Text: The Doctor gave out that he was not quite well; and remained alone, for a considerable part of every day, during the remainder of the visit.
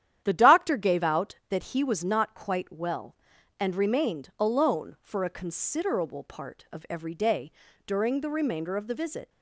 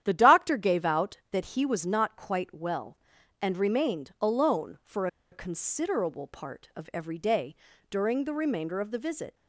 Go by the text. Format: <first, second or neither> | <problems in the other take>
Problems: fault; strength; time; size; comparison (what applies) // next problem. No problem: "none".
first | starts louder than the rest; strong; until 1.0 s; 10.5 dB; strong in the first // pauses between "for" and "a"; slight; at 5.0 s; 0.24 s long